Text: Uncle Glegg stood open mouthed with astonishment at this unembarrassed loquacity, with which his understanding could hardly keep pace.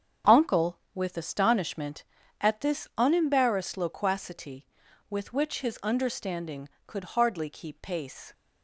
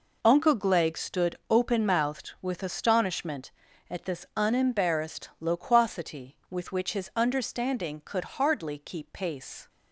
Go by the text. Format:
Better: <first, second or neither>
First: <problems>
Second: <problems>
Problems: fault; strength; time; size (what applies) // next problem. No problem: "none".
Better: second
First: starts louder than the rest; strong; until 1.4 s; 8 dB // skips "Glegg stood open mouthed"; at 0.8 s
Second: none